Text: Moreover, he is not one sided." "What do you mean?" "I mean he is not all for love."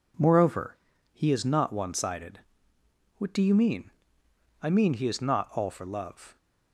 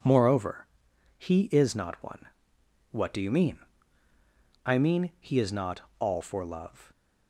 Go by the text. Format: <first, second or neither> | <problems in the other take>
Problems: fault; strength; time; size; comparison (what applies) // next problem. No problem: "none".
first | skips "sided"; at 2.5 s // pauses between "not" and "all"; slight; at 5.8 s; 0.18 s long